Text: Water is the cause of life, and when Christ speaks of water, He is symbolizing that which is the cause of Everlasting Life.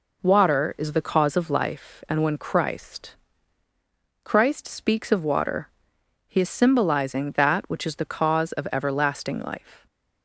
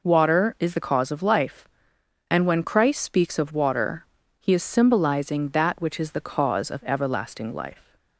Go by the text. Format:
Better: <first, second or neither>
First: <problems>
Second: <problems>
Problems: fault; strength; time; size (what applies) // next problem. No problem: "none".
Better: second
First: says "Christ" twice; at 4.2 s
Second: none